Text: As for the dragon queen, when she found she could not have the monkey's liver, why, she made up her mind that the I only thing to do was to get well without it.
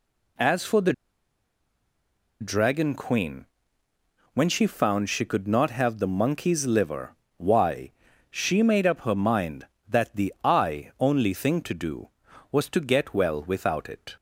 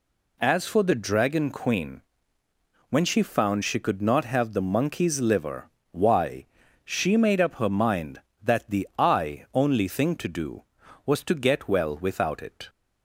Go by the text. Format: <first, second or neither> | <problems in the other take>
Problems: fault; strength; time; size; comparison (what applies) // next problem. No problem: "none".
second | pauses between "the" and "dragon"; strong; at 0.9 s; 1.4 s long